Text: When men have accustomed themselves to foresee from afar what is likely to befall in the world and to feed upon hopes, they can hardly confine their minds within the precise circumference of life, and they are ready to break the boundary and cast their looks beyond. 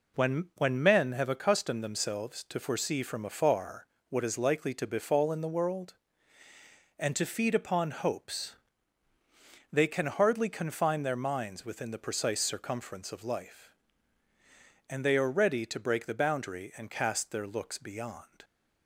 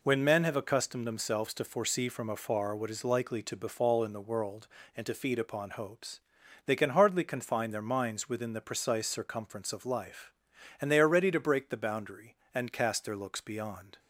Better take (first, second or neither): second